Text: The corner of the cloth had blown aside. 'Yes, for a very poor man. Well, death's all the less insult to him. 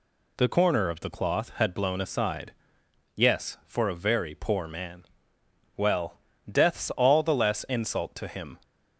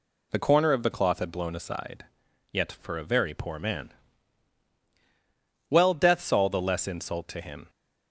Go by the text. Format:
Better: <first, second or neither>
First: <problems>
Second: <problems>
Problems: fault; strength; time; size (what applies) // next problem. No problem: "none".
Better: first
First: none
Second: says "Yet" for "Yes"; at 2.5 s